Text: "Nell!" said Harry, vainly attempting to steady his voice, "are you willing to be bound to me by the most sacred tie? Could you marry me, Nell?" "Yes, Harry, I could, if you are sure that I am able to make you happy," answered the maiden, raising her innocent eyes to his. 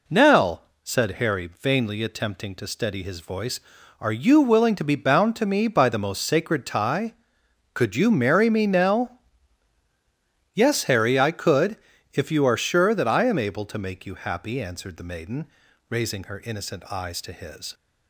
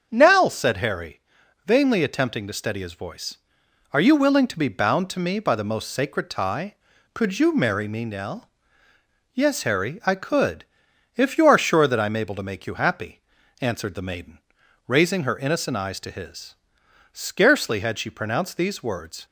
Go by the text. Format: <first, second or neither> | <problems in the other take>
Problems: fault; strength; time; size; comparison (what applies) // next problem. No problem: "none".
first | starts louder than the rest; until 1.1 s; 7 dB // goes on to say "Scarcely had she pronounced these words"; strong; from 17.1 s on; 2.1 s long